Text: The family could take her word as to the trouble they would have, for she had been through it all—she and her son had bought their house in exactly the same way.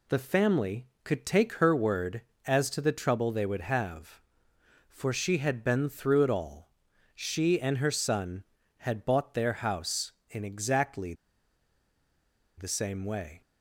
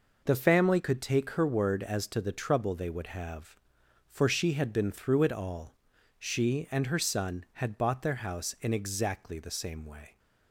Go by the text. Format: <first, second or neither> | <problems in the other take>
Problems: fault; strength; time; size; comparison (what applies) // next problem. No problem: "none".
second | pauses between "exactly" and "the"; strong; at 11.1 s; 1.4 s long